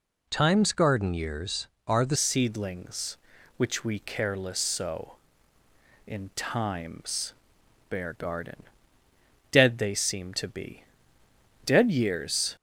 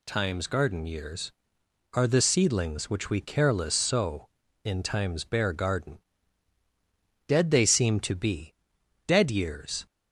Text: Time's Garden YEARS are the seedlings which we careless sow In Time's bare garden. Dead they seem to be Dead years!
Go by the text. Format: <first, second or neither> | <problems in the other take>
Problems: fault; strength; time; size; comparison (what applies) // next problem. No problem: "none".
second | changes voice at "seedlings"; from 2.1 s on; 10.4 s long // pauses between "Time's" and "bare"; noticeable; at 7.3 s; 0.56 s long // pauses between "be" and "Dead"; noticeable; at 10.8 s; 0.82 s long; noticeable in the second